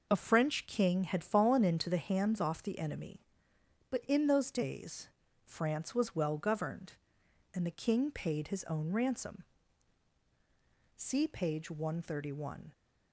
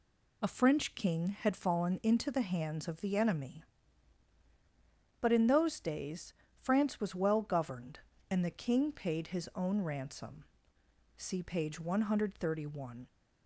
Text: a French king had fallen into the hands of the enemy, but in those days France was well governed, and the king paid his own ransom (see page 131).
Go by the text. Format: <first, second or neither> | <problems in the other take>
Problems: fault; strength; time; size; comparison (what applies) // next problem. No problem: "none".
second | says "off" for "of"; at 2.4 s // pauses between "days" and "France"; slight; at 5.0 s; 0.36 s long; slight in the second